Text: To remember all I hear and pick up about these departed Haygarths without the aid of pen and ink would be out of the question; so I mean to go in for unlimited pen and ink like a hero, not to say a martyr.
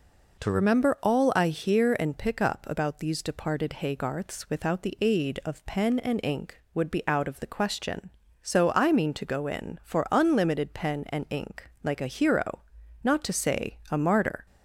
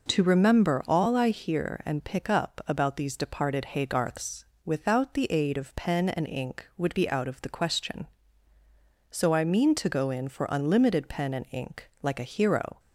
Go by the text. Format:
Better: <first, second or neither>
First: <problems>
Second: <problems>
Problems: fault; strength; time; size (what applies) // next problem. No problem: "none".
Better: first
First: none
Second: pauses between "Haygarths" and "without"; slight; at 4.4 s; 0.20 s long // stops before "not to say a martyr"; at 12.7 s